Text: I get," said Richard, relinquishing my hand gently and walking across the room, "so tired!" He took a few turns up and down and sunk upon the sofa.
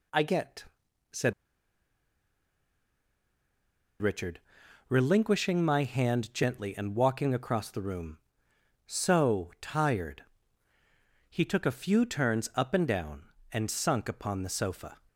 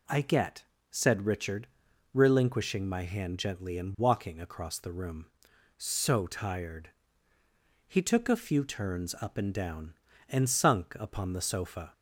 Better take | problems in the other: second | pauses between "said" and "Richard"; strong; at 1.3 s; 2.6 s long

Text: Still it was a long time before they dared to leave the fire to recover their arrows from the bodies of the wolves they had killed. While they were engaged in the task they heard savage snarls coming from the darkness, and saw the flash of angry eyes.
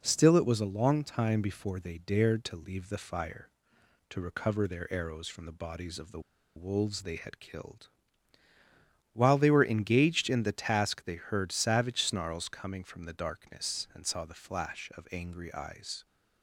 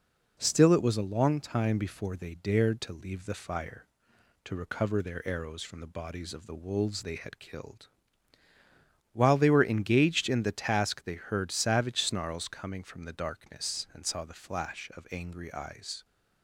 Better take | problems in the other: second | pauses between "the" and "wolves"; at 6.1 s; 0.36 s long

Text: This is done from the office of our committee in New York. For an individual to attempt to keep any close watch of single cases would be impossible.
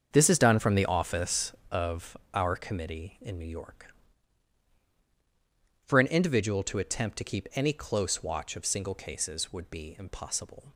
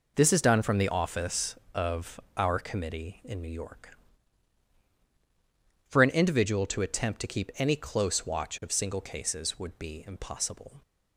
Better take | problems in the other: second | starts louder than the rest; until 1.9 s; 7 dB // pauses between "of" and "our"; slight; at 2.1 s; 0.16 s long; slight in the second

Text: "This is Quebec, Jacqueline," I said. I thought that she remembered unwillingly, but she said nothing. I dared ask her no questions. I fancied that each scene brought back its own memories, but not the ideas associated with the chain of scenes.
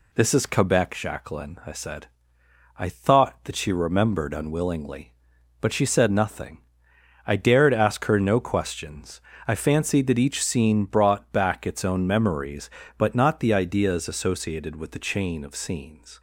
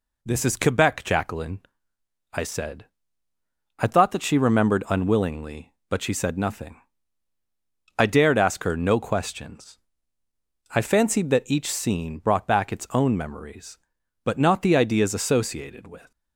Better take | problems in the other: first | stops before "the chain of scenes"; at 16.1 s

